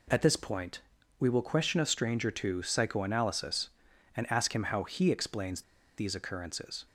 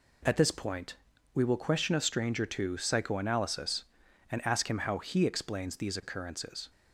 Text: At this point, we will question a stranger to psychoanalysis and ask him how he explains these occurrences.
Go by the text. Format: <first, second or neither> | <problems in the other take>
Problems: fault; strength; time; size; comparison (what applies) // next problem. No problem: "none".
second | pauses between "explains" and "these"; slight; at 5.6 s; 0.34 s long